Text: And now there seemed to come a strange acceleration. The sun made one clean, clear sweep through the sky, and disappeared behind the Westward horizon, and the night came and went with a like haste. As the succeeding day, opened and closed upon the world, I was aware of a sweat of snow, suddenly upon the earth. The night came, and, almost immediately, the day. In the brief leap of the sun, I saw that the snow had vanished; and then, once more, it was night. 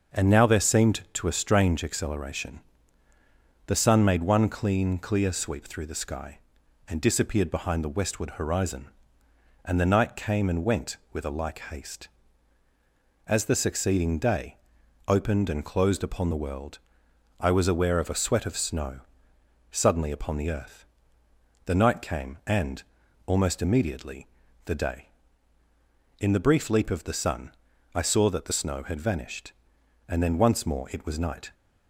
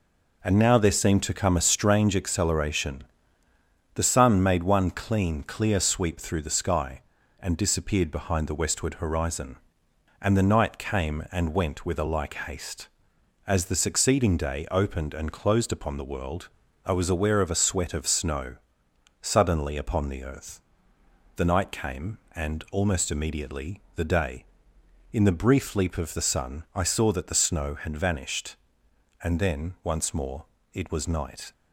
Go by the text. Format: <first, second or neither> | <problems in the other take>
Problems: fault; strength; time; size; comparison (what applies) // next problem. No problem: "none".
second | starts louder than the rest; until 1.2 s; 6.5 dB // skips "come"; at 1.2 s